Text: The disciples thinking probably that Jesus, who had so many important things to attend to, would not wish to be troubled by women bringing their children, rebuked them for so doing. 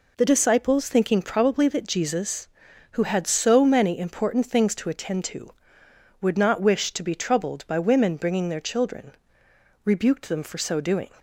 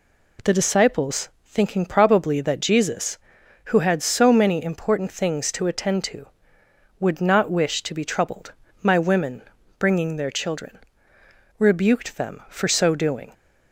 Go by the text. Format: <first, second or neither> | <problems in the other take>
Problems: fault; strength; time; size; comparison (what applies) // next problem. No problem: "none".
first | pauses between "disciples" and "thinking"; slight; at 1.2 s; 0.16 s long // says "my" for "by"; at 8.8 s // pauses between "women" and "bringing"; slight; at 9.4 s; 0.36 s long